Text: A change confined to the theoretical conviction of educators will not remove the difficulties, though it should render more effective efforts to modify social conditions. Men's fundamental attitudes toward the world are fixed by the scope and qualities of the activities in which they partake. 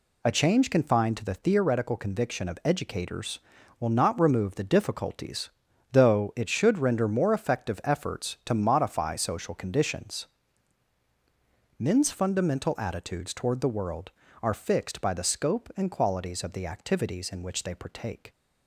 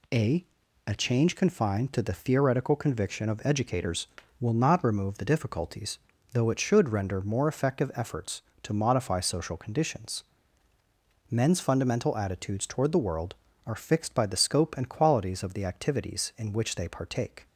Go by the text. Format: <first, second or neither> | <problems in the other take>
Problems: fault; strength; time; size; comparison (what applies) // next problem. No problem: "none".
first | says "A" twice; at 0.8 s